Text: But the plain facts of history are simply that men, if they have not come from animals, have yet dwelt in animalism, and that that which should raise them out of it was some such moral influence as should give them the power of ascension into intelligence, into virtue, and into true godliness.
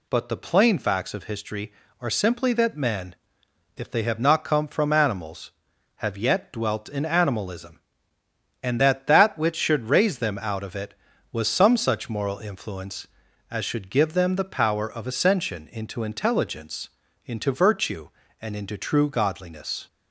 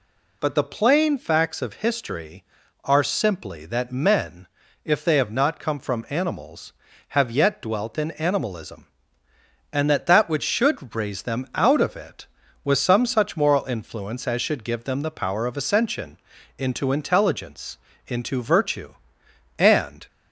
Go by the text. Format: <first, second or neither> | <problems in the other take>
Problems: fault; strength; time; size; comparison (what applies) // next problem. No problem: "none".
first | pauses between "ascension" and "into"; at 16.1 s; 0.42 s long // stops before "into true godliness"; at 20.0 s